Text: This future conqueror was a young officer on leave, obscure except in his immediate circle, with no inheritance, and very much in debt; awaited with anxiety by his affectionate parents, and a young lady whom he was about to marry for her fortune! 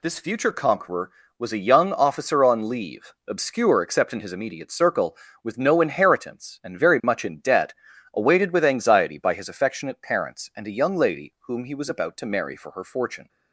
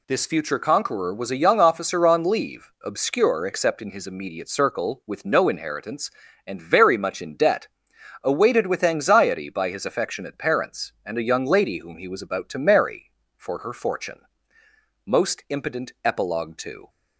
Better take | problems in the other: first | goes on to say "Most impotent epilogue to"; strong; from 15.0 s on; 1.8 s long

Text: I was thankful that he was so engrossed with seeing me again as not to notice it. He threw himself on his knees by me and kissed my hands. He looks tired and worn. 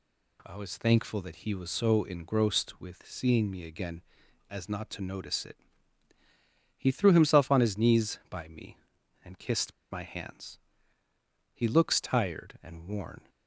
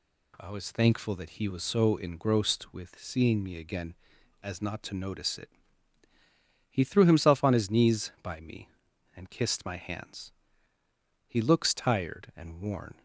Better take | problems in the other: second | pauses between "kissed" and "my"; slight; at 9.7 s; 0.18 s long

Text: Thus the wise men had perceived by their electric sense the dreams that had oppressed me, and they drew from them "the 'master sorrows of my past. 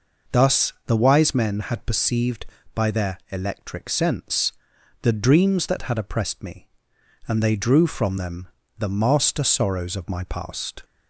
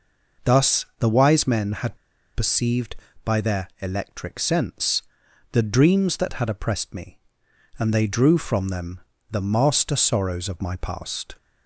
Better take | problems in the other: first | pauses between "had" and "perceived"; at 1.9 s; 0.37 s long // pauses between "sense" and "the"; noticeable; at 5.0 s; 0.48 s long; noticeable in the first // pauses between "them" and "the"; slight; at 8.9 s; 0.32 s long; slight in the first

